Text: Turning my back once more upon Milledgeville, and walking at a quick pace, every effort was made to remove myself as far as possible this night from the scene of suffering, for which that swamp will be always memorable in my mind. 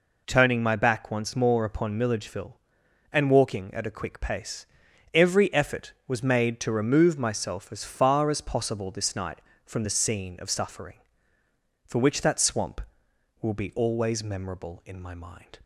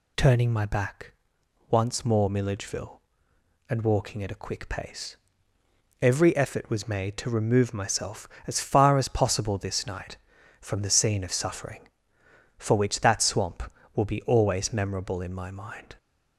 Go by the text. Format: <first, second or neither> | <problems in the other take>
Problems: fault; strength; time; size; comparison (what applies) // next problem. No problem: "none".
first | pauses between "back" and "once"; noticeable; at 1.1 s; 0.58 s long // skips "upon"; at 2.2 s